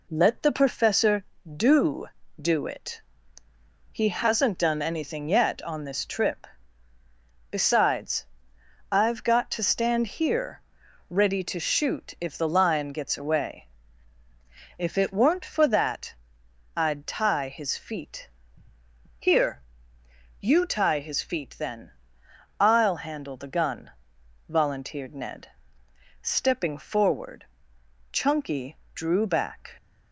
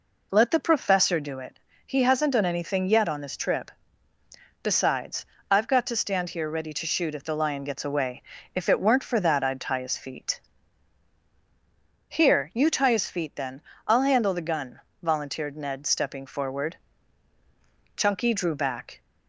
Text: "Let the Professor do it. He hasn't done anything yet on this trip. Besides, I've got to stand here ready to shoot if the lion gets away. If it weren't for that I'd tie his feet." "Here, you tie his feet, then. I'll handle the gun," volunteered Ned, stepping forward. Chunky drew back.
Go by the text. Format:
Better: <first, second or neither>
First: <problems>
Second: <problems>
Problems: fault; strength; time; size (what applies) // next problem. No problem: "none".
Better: second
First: says "do" twice; at 2.4 s // pauses between "here" and "ready"; noticeable; at 10.6 s; 0.48 s long // pauses between "that" and "I'd"; noticeable; at 16.1 s; 0.60 s long // pauses between "Chunky" and "drew"; slight; at 28.7 s; 0.20 s long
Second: none